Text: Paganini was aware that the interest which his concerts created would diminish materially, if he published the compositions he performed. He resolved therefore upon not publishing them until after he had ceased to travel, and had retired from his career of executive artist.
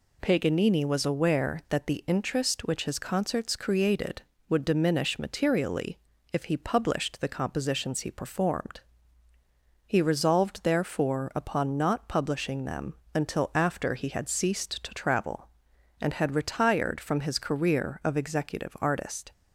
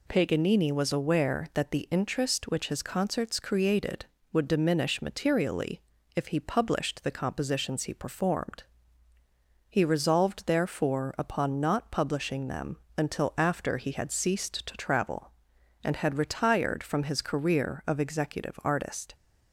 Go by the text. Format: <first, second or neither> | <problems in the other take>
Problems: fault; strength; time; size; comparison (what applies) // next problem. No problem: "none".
neither | pauses between "them" and "until"; slight; the same in both